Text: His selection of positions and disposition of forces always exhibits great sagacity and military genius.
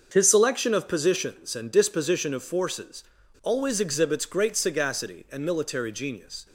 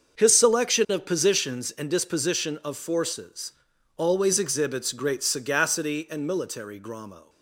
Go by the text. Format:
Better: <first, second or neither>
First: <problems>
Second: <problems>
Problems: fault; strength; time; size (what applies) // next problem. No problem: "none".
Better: first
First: starts louder than the rest; until 1.1 s; 6.5 dB // pauses between "forces" and "always"; at 3.0 s; 0.41 s long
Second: starts louder than the rest; until 1.2 s; 6.5 dB // pauses between "forces" and "always"; at 3.5 s; 0.42 s long // says "gramo" for "genius"; at 6.7 s